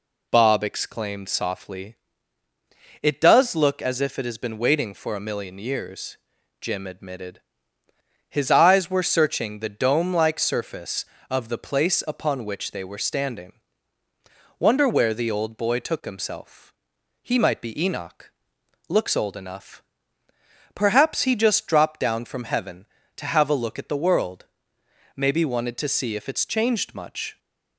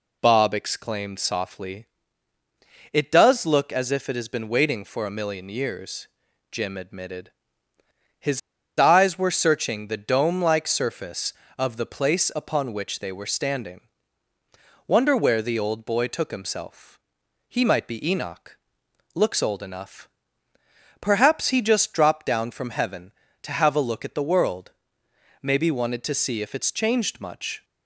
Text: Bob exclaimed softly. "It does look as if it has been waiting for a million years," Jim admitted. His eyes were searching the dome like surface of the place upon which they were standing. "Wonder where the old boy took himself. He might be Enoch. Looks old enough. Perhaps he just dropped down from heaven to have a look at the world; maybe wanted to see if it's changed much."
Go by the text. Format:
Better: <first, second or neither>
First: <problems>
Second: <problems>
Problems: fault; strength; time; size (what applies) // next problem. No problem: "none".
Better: first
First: none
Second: pauses between "His" and "eyes"; at 8.3 s; 0.38 s long